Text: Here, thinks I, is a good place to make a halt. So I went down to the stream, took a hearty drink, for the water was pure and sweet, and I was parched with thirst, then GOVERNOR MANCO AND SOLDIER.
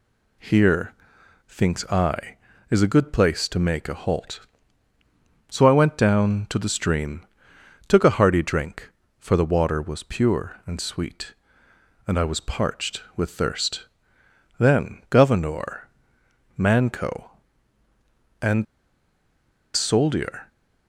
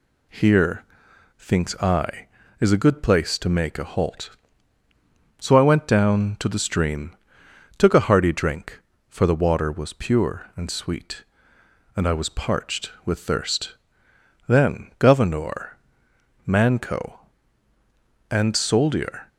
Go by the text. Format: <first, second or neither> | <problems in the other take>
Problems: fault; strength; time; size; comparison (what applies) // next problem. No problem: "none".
second | pauses between "GOVERNOR" and "MANCO"; noticeable; at 15.8 s; 0.70 s long; noticeable in the second // pauses between "AND" and "SOLDIER"; at 18.6 s; 1.1 s long